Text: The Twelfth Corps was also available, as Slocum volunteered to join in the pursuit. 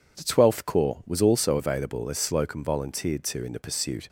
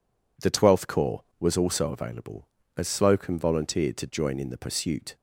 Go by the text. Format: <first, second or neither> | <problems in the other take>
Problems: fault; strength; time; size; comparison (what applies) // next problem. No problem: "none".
second | skips "join"; at 3.4 s